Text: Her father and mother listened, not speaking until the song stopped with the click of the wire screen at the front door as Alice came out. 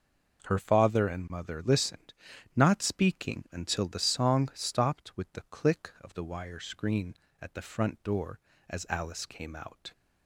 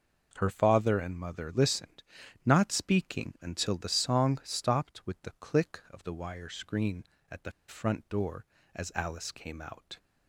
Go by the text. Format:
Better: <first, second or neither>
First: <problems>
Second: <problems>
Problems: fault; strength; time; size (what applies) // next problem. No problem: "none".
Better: first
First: none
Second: pauses between "the" and "front"; slight; at 7.5 s; 0.16 s long